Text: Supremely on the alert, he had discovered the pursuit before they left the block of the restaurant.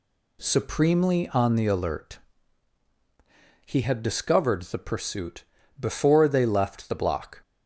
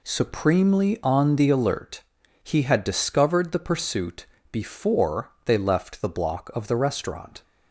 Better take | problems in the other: second | pauses between "pursuit" and "before"; slight; at 5.4 s; 0.34 s long; slight in the second // stops before "of the restaurant"; at 7.4 s

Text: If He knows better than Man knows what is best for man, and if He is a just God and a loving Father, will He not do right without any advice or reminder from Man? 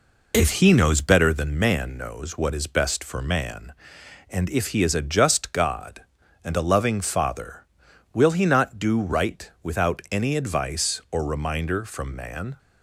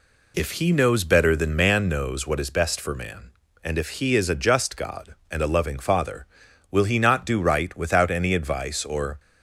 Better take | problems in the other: first | stops before "reminder from Man"; at 9.1 s

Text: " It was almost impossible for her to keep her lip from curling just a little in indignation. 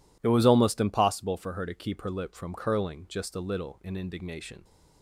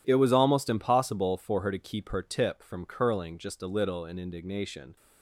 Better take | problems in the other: first | says "tip" for "lip"; at 2.2 s

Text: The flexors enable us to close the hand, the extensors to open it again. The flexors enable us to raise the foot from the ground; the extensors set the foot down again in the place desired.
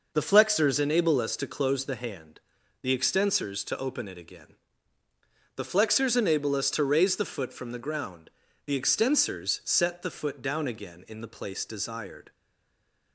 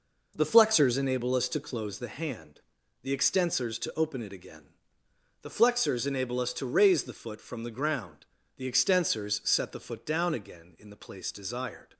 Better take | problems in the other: second | stays silent after the last word; slight; from 12.3 s on; 0.8 s long

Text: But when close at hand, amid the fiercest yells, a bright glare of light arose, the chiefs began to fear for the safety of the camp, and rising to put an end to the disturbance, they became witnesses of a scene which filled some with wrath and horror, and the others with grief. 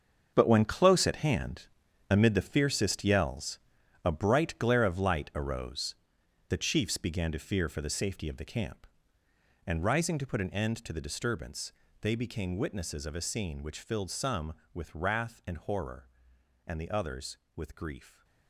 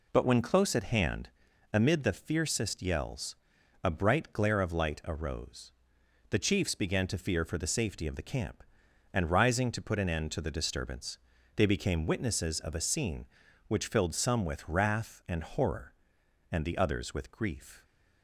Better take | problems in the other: second | gets quieter; strong; throughout; 12 dB

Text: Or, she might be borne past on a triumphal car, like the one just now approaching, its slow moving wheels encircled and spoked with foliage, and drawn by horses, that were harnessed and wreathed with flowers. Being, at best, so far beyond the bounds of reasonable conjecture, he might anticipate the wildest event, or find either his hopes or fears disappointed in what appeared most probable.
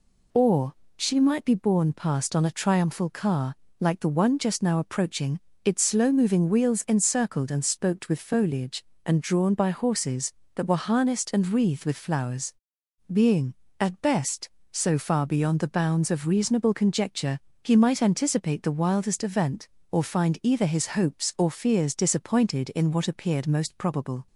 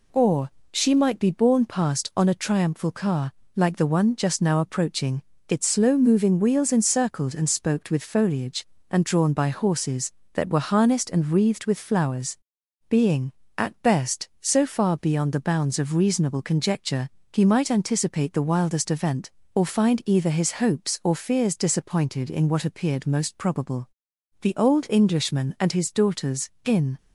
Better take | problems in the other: first | goes on to say "The old Englishman and his daughters in"; strong; from 24.4 s on; 2.5 s long

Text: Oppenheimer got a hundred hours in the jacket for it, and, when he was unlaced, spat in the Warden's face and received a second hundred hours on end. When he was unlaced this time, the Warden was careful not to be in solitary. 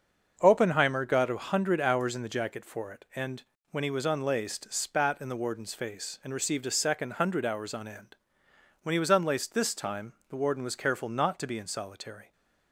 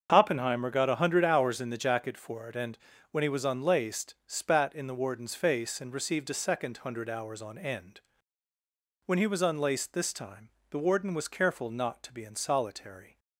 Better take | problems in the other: neither | starts louder than the rest; the same in both

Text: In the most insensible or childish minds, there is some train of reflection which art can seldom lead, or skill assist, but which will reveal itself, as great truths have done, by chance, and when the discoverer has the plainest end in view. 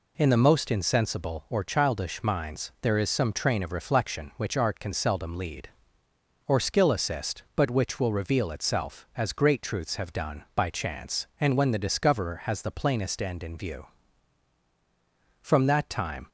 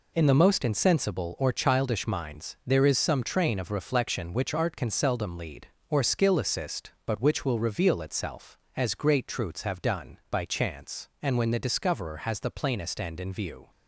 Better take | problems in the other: second | goes on to say "From that time"; noticeable; from 15.4 s on; 0.86 s long

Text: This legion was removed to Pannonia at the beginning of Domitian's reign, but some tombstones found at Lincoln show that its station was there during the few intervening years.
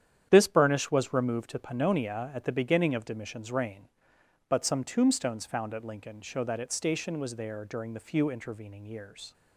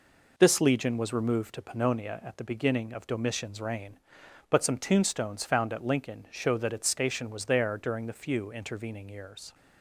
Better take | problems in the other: second | starts louder than the rest; strong; until 1.3 s; 9.5 dB // says "burnish" for "legion"; at 0.4 s

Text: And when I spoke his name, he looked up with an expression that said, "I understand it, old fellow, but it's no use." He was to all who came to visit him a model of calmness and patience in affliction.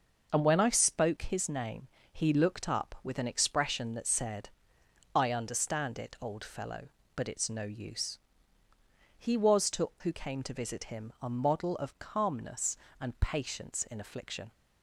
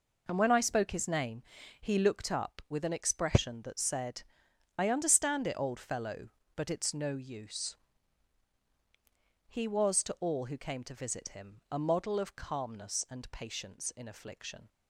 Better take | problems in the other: second | skips "all"; at 9.9 s

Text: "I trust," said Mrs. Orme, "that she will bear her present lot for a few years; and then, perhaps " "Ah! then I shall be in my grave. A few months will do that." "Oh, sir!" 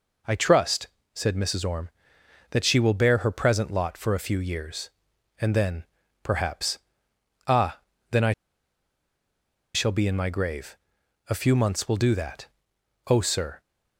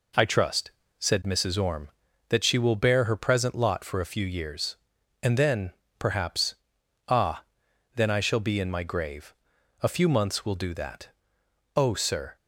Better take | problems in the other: second | pauses between "I" and "shall"; strong; at 8.3 s; 1.4 s long

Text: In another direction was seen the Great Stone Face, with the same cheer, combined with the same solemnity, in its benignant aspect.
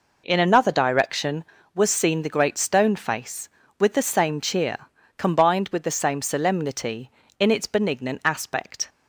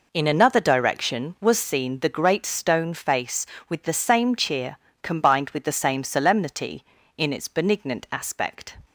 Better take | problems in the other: neither | none

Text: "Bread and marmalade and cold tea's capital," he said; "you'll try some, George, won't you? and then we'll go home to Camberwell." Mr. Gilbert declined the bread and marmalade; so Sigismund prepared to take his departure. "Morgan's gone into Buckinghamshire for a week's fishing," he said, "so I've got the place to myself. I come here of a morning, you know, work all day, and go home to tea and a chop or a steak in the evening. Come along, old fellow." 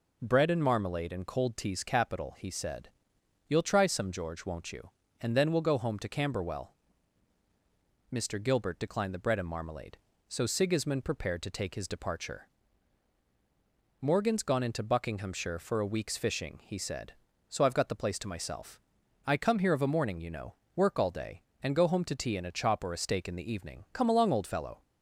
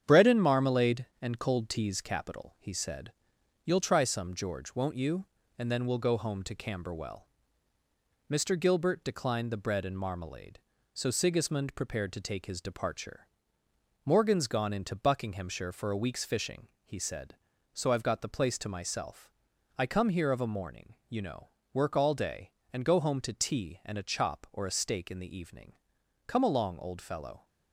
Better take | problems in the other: first | gets quieter; noticeable; throughout; 5.5 dB

